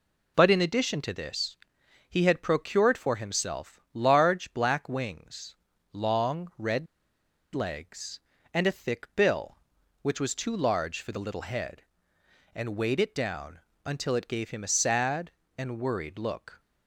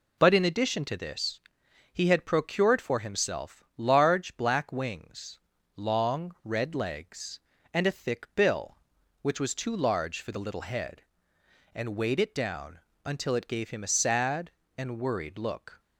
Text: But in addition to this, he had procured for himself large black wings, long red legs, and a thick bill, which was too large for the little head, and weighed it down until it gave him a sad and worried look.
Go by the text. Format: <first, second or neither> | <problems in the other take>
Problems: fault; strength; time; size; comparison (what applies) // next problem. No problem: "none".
second | pauses between "red" and "legs"; noticeable; at 6.8 s; 0.67 s long // pauses between "down" and "until"; slight; at 13.5 s; 0.24 s long; slight in the second